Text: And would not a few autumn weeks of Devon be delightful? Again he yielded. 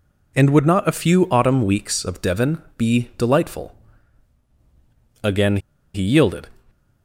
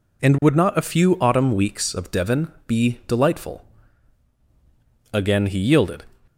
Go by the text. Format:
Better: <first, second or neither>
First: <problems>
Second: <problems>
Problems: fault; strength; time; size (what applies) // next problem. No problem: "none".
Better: second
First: pauses between "Devon" and "be"; slight; at 2.6 s; 0.16 s long // pauses between "Again" and "he"; at 5.5 s; 0.36 s long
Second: pauses between "Devon" and "be"; slight; at 2.4 s; 0.16 s long